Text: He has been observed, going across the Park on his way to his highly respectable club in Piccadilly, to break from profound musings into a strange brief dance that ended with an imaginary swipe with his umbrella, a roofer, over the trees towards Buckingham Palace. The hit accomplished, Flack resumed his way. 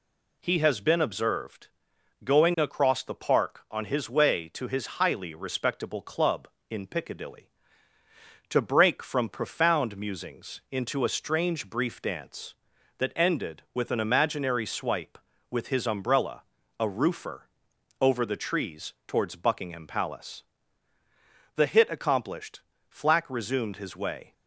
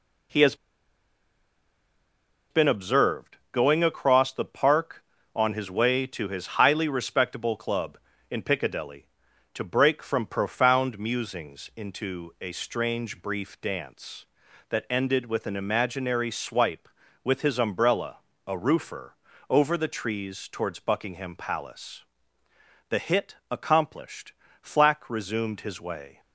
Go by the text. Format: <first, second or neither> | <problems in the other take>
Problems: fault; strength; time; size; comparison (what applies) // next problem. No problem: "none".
first | pauses between "has" and "been"; strong; at 0.5 s; 1.9 s long